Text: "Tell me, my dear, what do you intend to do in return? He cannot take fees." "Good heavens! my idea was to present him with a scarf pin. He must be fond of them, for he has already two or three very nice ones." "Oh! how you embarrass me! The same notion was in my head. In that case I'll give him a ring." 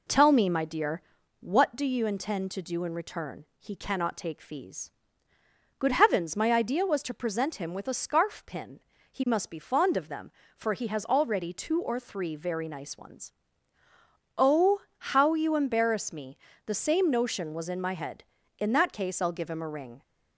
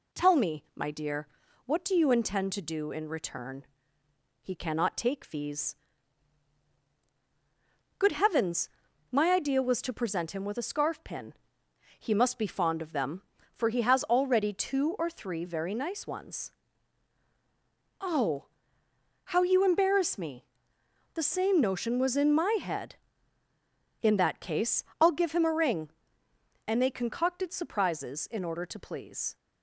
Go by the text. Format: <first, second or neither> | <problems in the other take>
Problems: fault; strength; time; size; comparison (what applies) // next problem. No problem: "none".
first | pauses between "case" and "I'll"; slight; at 24.8 s; 0.16 s long // goes on to say "And they concocted surprises in order to please"; strong; from 26.6 s on; 2.7 s long